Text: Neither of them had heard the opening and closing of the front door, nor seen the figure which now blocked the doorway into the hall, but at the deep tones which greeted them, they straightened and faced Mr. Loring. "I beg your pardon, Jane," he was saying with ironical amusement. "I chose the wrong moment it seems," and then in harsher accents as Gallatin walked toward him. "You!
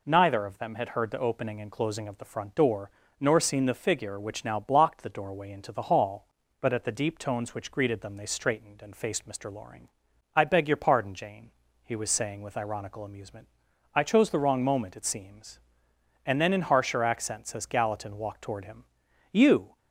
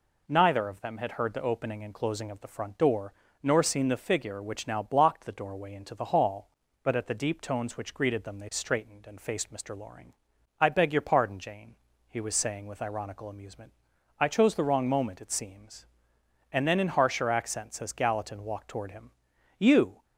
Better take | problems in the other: neither | none

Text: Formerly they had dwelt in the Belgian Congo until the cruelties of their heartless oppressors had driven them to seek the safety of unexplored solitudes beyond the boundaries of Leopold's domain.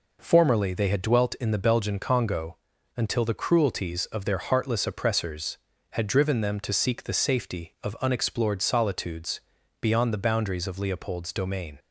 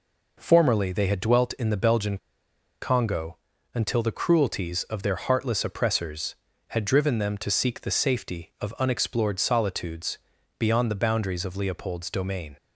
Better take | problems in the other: first | pauses between "Belgian" and "Congo"; noticeable; at 2.1 s; 0.64 s long // pauses between "Congo" and "until"; slight; at 3.3 s; 0.36 s long; also in the first // pauses between "solitudes" and "beyond"; at 10.1 s; 0.40 s long; also in the first

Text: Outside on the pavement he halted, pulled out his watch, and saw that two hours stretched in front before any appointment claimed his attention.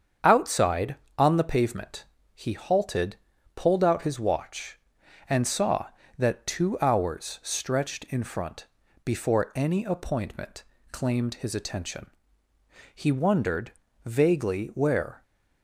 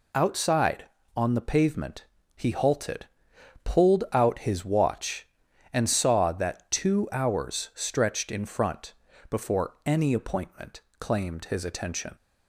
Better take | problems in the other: second | starts louder than the rest; strong; until 1.4 s; 7.5 dB // pauses between "pavement" and "he"; slight; at 2.0 s; 0.30 s long; slight in the second // pauses between "front" and "before"; at 8.6 s; 0.38 s long; slight in the second // pauses between "appointment" and "claimed"; slight; at 10.6 s; 0.26 s long; slight in the second // goes on to say "He wondered vaguely where"; strong; from 12.9 s on; 2.2 s long

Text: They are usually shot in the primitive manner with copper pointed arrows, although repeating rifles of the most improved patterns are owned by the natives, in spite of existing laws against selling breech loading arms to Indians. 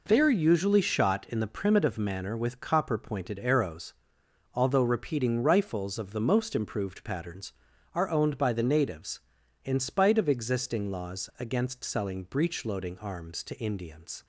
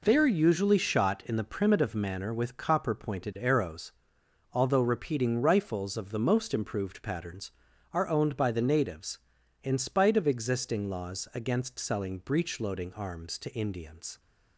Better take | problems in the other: neither | none

